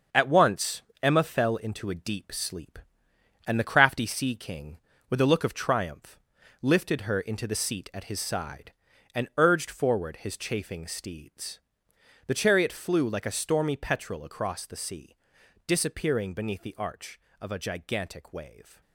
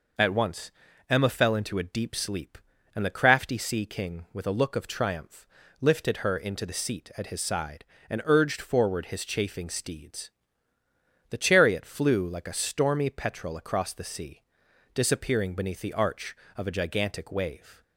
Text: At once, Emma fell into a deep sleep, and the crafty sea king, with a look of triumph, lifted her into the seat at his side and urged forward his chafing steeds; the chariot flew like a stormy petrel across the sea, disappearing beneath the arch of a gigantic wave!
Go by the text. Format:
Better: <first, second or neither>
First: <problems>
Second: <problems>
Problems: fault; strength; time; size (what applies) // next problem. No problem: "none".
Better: second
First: gets quieter; strong; throughout; 7.5 dB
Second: none